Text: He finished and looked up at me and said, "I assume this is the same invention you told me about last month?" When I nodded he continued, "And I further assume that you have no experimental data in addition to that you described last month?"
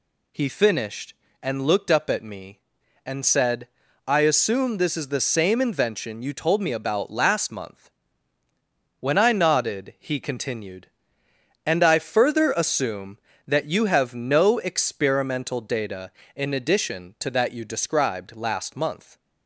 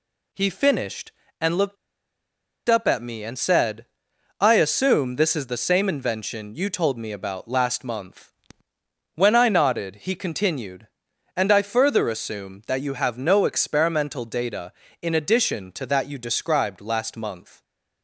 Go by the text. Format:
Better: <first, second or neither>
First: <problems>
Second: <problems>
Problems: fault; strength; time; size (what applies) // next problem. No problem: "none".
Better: first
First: none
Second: pauses between "looked" and "up"; noticeable; at 1.7 s; 0.92 s long